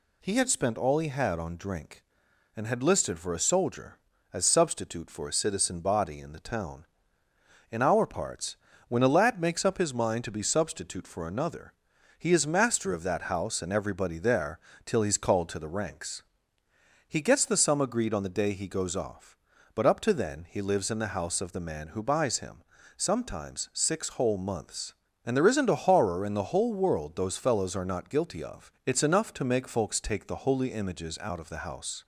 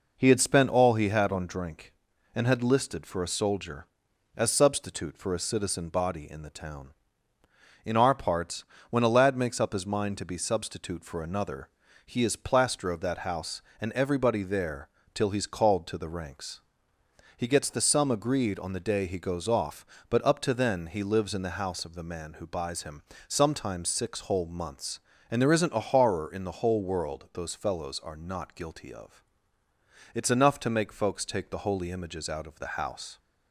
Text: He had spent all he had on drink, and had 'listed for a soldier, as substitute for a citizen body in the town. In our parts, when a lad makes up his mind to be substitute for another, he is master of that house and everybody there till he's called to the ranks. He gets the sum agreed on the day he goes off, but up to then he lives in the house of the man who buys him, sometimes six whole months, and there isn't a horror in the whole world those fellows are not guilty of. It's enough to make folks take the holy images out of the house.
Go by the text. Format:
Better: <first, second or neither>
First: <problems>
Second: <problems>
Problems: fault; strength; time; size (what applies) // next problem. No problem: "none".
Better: first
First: pauses between "there" and "till"; slight; at 14.5 s; 0.26 s long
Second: says "plaster" for "master"; at 12.3 s // pauses between "there" and "till"; slight; at 14.8 s; 0.26 s long